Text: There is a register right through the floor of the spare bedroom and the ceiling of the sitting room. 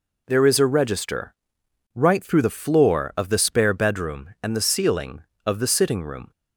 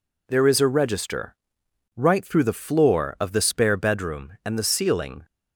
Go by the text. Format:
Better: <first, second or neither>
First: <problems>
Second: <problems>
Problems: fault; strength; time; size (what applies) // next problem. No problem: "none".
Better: first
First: pauses between "register" and "right"; noticeable; at 1.3 s; 0.62 s long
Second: pauses between "register" and "right"; noticeable; at 1.3 s; 0.62 s long // stops before "of the sitting room"; at 5.2 s